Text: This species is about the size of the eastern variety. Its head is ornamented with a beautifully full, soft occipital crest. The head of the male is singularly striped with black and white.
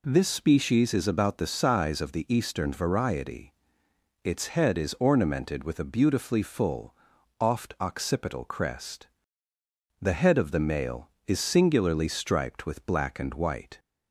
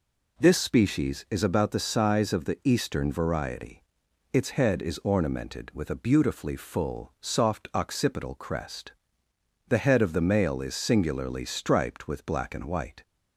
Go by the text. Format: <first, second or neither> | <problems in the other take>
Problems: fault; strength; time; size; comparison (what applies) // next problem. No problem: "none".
second | says "oft" for "soft"; at 7.4 s